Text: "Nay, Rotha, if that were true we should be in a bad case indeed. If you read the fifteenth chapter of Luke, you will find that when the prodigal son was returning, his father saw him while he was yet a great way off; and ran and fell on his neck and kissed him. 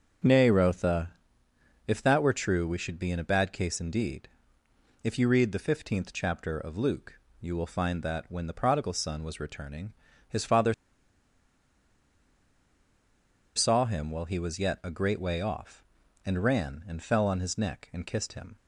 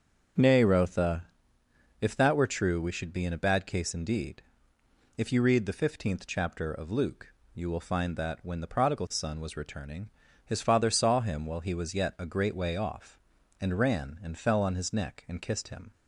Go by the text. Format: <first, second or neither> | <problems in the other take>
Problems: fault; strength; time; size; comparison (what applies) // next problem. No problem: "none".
second | starts louder than the rest; until 1.9 s; 7 dB; also in the second // pauses between "father" and "saw"; strong; at 10.7 s; 2.8 s long